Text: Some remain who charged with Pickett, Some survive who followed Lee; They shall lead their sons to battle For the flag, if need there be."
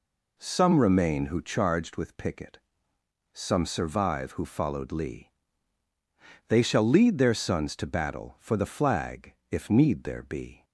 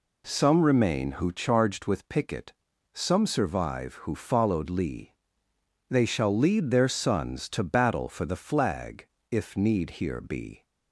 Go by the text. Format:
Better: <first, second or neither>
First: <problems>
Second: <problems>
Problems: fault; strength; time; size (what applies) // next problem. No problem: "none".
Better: first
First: none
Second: says "here" for "there"; at 10.0 s